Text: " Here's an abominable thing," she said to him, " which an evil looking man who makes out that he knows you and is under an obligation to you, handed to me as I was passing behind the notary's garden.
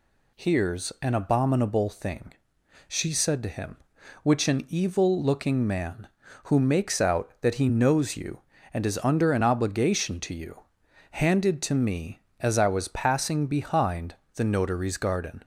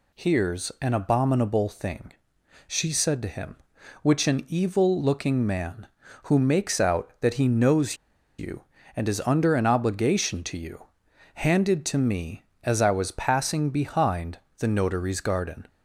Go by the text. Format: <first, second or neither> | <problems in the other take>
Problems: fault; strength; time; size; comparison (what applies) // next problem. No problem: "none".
first | pauses between "knows" and "you"; at 7.9 s; 0.43 s long // pauses between "behind" and "the"; slight; at 14.3 s; 0.22 s long; slight in the first